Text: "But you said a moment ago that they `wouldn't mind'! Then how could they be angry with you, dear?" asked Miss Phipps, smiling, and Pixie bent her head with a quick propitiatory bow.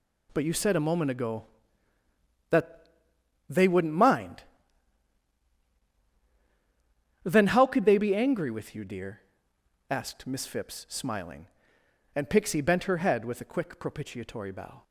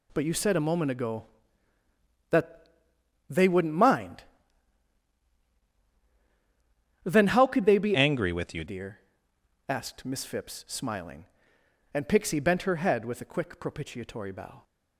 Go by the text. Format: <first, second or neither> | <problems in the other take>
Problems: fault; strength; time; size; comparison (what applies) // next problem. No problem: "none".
first | pauses between "that" and "they"; noticeable; at 2.6 s; 0.64 s long; noticeable in the first // changes voice from "angry" to "you"; from 7.9 to 8.6 s; 0.7 s long